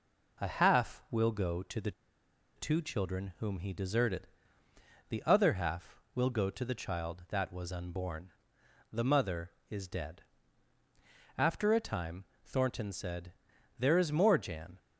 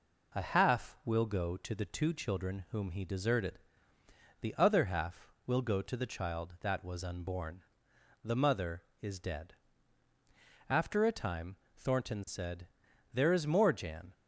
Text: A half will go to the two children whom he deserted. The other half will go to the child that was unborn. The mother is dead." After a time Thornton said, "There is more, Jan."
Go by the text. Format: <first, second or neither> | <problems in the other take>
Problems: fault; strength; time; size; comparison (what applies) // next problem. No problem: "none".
second | pauses between "the" and "two"; noticeable; at 1.9 s; 0.65 s long // pauses between "time" and "Thornton"; slight; at 12.2 s; 0.18 s long; slight in the second